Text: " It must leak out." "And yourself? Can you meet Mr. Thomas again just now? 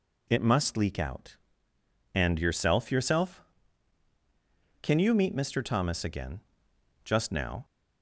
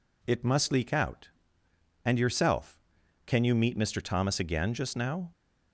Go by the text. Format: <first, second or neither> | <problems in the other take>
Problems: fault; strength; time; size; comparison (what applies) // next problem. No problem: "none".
second | says "yourself" twice; at 2.9 s // pauses between "again" and "just"; noticeable; at 6.4 s; 0.62 s long